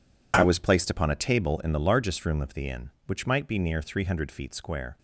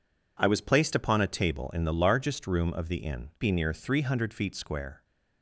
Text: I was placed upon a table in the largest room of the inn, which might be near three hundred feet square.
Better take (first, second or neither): first